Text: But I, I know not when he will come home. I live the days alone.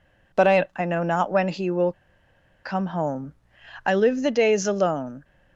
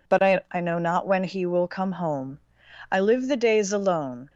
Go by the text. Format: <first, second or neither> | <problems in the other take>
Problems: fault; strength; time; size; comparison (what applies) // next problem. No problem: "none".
second | pauses between "will" and "come"; noticeable; at 1.9 s; 0.72 s long